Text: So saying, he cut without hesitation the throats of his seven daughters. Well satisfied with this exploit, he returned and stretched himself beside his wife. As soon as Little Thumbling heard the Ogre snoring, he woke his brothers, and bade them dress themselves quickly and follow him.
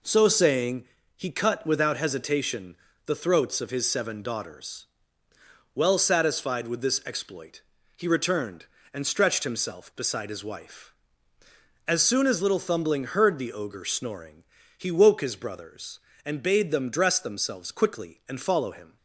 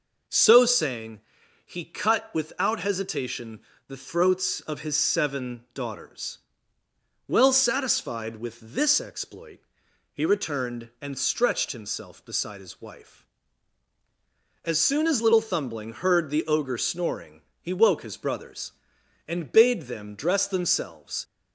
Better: first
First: pauses between "hesitation" and "the"; slight; at 2.7 s; 0.30 s long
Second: pauses between "hesitation" and "the"; slight; at 3.5 s; 0.28 s long // stops before "quickly and follow him"; at 21.2 s

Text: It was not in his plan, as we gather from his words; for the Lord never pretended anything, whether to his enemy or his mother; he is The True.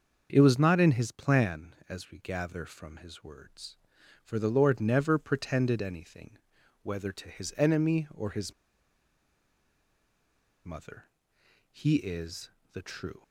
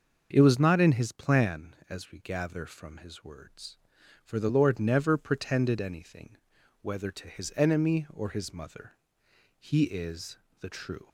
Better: second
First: starts louder than the rest; until 1.3 s; 6.5 dB // pauses between "his" and "mother"; strong; at 8.5 s; 2.1 s long // pauses between "is" and "The"; slight; at 12.5 s; 0.22 s long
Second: starts louder than the rest; until 1.3 s; 6.5 dB // pauses between "is" and "The"; slight; at 10.3 s; 0.22 s long

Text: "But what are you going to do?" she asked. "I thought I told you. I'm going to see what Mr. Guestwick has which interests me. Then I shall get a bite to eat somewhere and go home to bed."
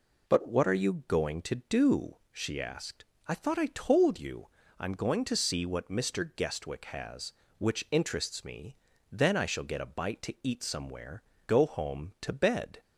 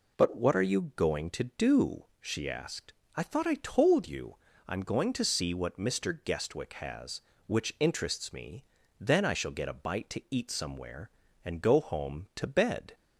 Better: second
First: skips "and"; at 11.3 s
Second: none

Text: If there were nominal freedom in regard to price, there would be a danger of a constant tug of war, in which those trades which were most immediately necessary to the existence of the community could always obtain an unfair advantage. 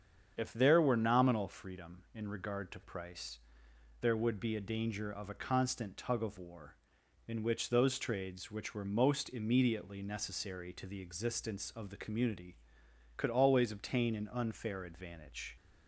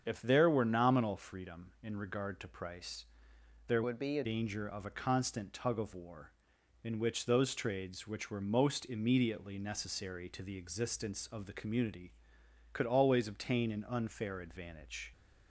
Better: first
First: starts louder than the rest; strong; until 1.3 s; 7.5 dB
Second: starts louder than the rest; strong; until 1.0 s; 7.5 dB // changes voice from "would" to "a"; from 3.8 to 4.2 s; 0.4 s long

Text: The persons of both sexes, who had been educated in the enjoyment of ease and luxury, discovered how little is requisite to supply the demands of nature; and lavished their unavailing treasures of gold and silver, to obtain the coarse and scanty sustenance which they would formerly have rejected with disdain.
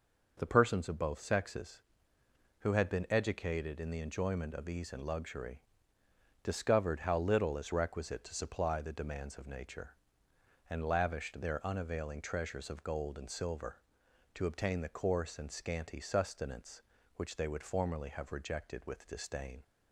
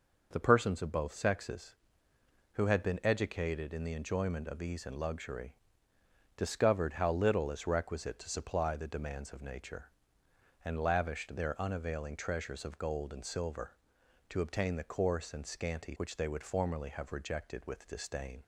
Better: first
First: none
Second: skips "sustenance"; at 15.9 s

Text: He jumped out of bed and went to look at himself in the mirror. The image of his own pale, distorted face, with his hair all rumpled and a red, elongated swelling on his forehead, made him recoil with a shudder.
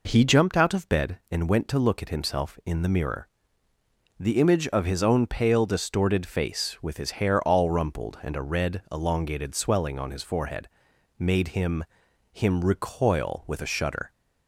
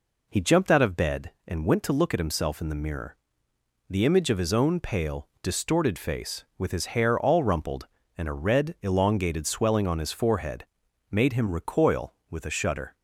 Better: second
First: says "him" twice; at 12.3 s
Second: none

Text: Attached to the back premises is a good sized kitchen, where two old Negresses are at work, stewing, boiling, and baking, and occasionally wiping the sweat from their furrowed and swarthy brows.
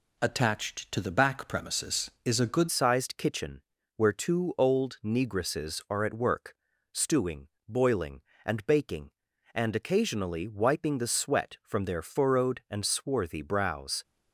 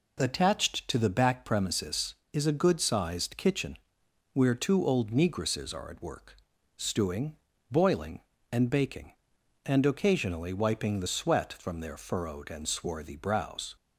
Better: second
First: changes voice at "sized"; from 2.7 s on; 11.3 s long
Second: none

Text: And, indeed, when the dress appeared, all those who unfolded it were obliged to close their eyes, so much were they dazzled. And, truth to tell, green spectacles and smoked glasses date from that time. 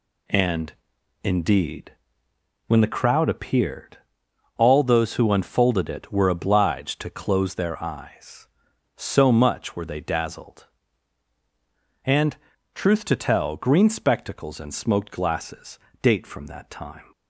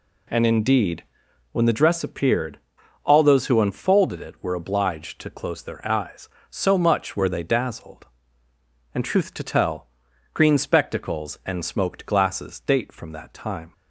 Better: second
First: says "crowd" for "dress"; at 2.8 s // pauses between "glasses" and "date"; slight; at 15.7 s; 0.24 s long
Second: none

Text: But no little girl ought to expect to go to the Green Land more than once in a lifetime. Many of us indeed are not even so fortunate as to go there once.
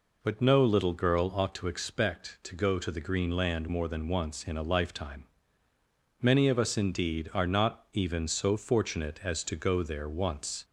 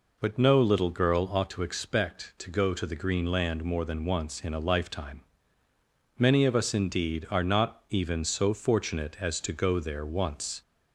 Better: neither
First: none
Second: none

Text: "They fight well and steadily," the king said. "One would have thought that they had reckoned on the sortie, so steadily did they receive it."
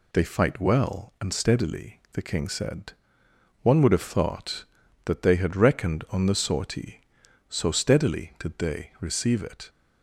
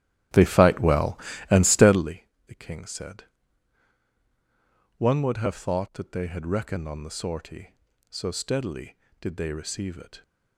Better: first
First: none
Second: starts louder than the rest; strong; until 2.2 s; 13 dB

